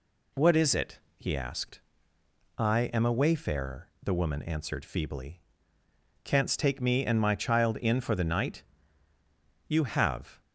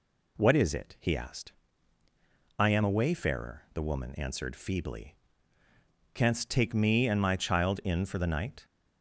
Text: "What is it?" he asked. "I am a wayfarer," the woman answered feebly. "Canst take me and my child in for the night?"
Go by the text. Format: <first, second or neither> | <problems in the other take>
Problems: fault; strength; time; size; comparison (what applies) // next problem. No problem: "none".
second | goes on to say "You have"; noticeable; from 9.6 s on; 0.74 s long